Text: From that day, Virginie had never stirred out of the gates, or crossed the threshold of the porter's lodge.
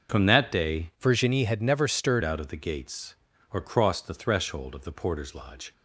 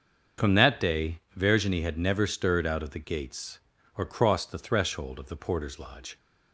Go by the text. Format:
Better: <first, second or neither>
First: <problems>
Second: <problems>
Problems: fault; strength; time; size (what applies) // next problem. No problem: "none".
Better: second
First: starts louder than the rest; until 1.2 s; 6.5 dB // changes voice from "Virginie" to "stirred"; from 1.0 to 2.2 s; 1.2 s long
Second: starts louder than the rest; until 1.5 s; 6.5 dB